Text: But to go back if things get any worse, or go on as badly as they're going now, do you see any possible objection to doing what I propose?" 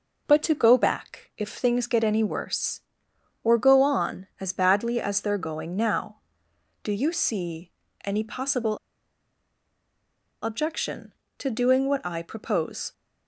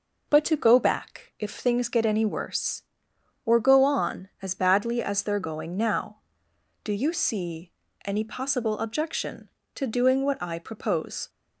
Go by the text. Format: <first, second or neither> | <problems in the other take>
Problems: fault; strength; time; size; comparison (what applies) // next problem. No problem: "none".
second | pauses between "see" and "any"; slight; at 7.7 s; 0.34 s long; slight in the second // pauses between "possible" and "objection"; strong; at 8.7 s; 1.6 s long